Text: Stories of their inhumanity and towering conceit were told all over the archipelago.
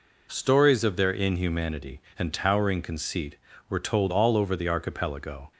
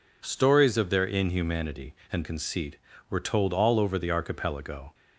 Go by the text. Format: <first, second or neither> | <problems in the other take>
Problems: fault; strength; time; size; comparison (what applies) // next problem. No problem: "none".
first | skips "towering"; at 2.2 s